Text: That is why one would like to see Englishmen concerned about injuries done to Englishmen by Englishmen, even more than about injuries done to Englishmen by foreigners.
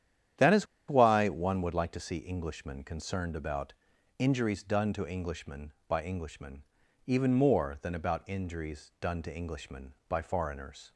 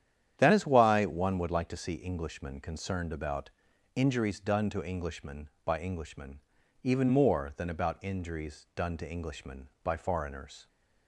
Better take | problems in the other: second | starts louder than the rest; strong; until 1.6 s; 10 dB; strong in the second // pauses between "is" and "why"; slight; at 0.6 s; 0.22 s long // pauses between "about" and "injuries"; at 3.7 s; 0.42 s long; also in the second

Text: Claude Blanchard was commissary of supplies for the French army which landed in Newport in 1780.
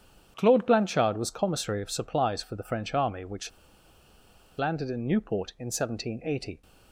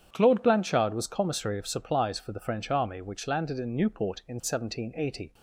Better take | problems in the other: second | starts louder than the rest; strong; until 1.3 s; 9 dB; strong in the second // pauses between "which" and "landed"; at 3.4 s; 1.0 s long

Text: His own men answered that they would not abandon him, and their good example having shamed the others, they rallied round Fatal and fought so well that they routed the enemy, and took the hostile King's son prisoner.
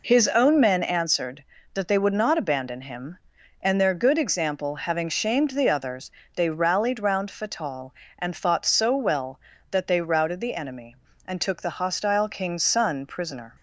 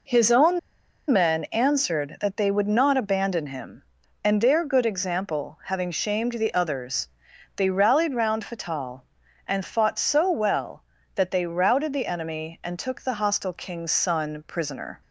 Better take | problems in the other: first | pauses between "own" and "men"; noticeable; at 0.5 s; 0.51 s long

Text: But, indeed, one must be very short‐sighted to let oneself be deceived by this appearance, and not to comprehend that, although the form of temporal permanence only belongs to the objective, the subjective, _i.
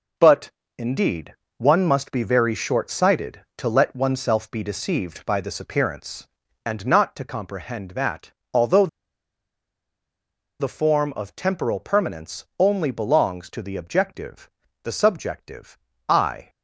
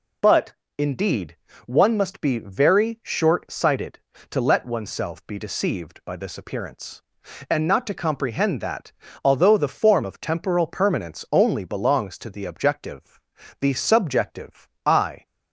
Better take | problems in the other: second | pauses between "although" and "the"; strong; at 8.8 s; 1.7 s long

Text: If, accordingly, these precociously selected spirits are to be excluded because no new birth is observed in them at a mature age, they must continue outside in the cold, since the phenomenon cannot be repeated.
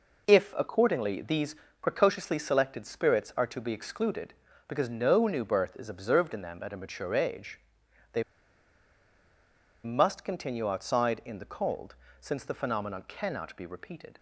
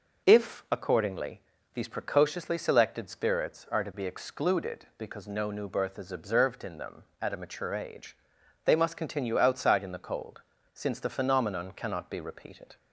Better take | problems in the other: second | pauses between "these" and "precociously"; slight; at 1.5 s; 0.24 s long // pauses between "they" and "must"; strong; at 8.2 s; 1.6 s long

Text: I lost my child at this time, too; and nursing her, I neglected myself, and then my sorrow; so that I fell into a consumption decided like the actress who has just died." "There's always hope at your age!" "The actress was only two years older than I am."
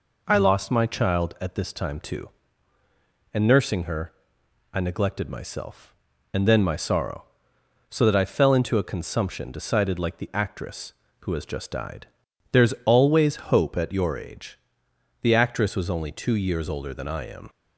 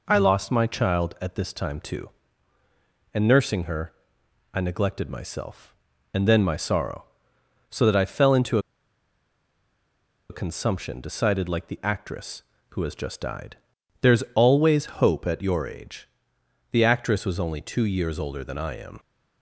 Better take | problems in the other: first | pauses between "into" and "a"; strong; at 8.5 s; 1.7 s long

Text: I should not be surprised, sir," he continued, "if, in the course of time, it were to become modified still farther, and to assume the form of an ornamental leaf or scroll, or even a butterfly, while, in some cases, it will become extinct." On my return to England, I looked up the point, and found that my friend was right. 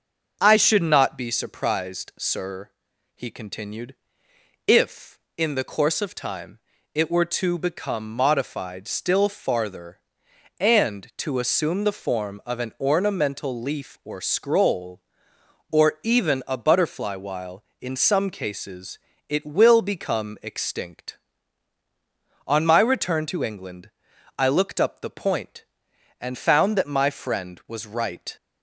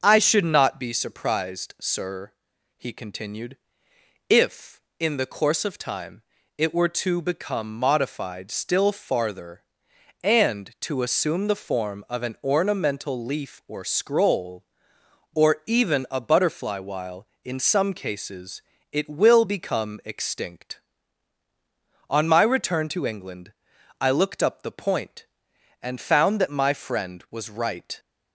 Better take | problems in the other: neither | none

